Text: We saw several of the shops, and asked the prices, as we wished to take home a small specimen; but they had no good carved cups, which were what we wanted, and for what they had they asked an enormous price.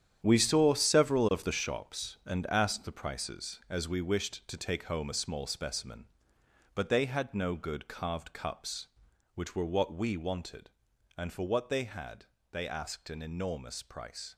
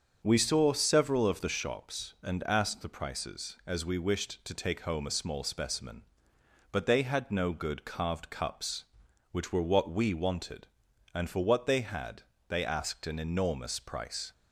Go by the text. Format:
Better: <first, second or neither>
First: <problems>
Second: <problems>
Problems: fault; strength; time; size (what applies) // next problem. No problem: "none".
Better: second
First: gets quieter; strong; throughout; 10.5 dB // starts louder than the rest; strong; until 1.2 s; 9.5 dB // pauses between "had" and "they"; slight; at 12.2 s; 0.28 s long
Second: starts louder than the rest; until 1.2 s; 7 dB // pauses between "had" and "they"; slight; at 12.2 s; 0.28 s long